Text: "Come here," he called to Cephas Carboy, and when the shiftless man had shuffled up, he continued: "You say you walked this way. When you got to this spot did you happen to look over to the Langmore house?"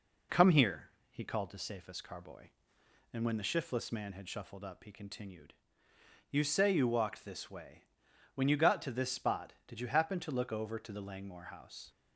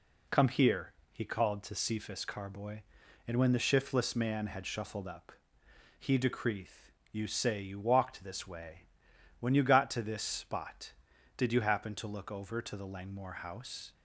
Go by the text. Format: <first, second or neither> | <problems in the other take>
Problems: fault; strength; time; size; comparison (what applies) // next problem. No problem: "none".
first | says "decreeth" for "continued"; at 6.1 s